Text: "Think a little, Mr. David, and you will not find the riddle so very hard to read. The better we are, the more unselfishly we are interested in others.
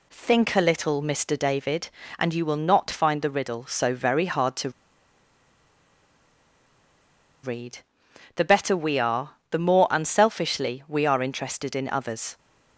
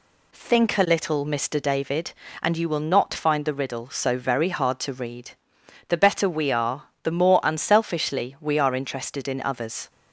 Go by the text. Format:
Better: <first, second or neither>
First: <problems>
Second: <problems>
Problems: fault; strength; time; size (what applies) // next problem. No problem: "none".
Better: second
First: pauses between "to" and "read"; strong; at 4.7 s; 2.7 s long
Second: none